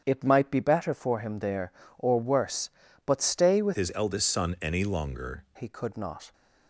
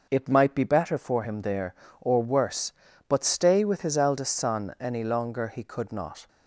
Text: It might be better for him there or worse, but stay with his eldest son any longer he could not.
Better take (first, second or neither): second